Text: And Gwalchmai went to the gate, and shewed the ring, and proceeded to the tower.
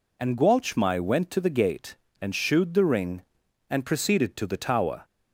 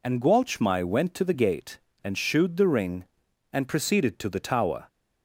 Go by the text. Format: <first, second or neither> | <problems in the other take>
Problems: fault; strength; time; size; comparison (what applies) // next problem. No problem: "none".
neither | none